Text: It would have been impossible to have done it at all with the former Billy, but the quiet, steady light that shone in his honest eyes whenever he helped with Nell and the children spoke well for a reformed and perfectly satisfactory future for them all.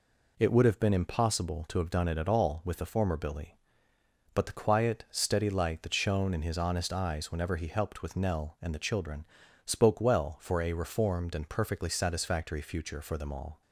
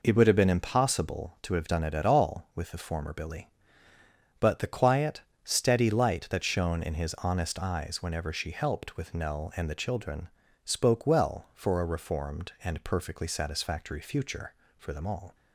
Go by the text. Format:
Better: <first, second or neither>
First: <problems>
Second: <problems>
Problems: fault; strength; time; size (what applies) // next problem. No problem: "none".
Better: first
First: pauses between "children" and "spoke"; at 9.2 s; 0.40 s long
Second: says "she" for "he"; at 8.3 s // pauses between "children" and "spoke"; slight; at 10.2 s; 0.36 s long